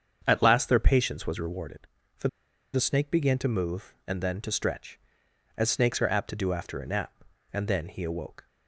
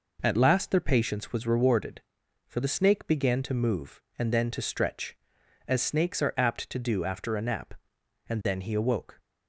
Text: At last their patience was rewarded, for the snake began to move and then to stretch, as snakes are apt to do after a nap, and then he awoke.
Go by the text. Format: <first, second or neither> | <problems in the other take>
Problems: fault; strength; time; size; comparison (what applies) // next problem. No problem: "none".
second | starts louder than the rest; strong; until 1.2 s; 7.5 dB // pauses between "for" and "the"; at 2.2 s; 0.44 s long